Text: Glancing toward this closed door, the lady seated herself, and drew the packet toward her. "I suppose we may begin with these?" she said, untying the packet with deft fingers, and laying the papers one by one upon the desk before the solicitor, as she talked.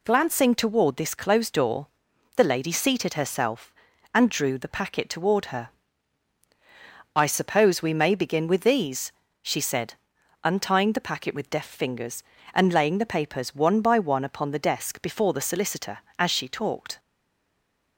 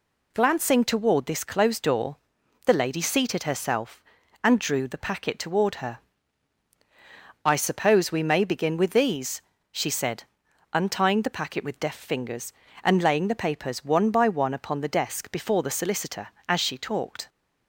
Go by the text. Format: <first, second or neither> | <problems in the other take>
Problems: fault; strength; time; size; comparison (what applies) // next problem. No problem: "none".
second | stays silent after the last word; from 16.9 s on; 1.0 s long